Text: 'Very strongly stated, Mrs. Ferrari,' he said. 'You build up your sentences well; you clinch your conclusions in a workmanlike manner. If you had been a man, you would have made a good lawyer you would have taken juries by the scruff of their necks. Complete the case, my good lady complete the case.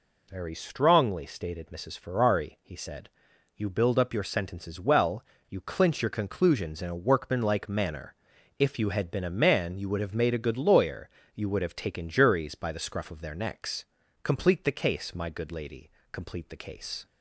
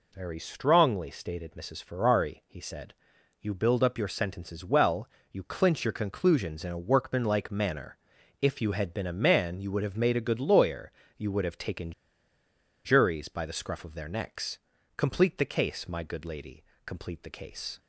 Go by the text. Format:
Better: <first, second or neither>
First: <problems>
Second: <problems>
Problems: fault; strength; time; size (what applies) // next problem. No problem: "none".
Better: first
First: pauses between "lawyer" and "you"; slight; at 11.0 s; 0.26 s long // pauses between "lady" and "complete"; slight; at 15.8 s; 0.22 s long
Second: pauses between "lawyer" and "you"; slight; at 10.9 s; 0.26 s long // pauses between "taken" and "juries"; noticeable; at 11.9 s; 0.93 s long // pauses between "lady" and "complete"; slight; at 16.6 s; 0.22 s long